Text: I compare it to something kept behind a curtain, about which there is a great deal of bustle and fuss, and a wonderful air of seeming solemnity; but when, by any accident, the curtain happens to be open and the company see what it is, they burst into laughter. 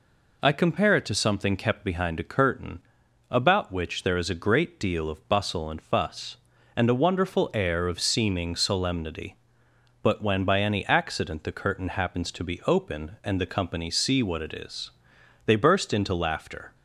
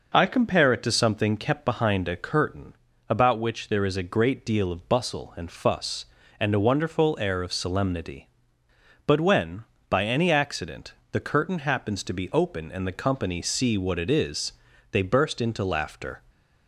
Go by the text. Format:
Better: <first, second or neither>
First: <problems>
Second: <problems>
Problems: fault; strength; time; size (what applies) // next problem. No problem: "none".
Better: first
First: none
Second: skips "seeming"; at 7.5 s